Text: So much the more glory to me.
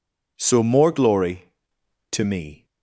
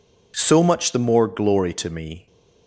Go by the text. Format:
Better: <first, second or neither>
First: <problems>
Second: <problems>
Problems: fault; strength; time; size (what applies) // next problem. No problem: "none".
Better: second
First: skips "much the"; at 0.6 s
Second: none